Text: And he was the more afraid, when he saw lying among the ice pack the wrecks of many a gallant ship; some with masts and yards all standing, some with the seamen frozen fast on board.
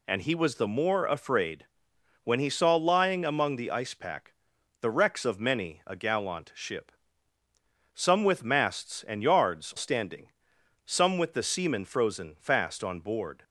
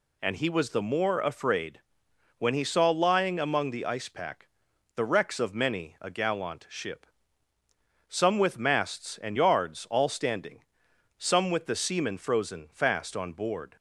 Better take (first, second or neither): second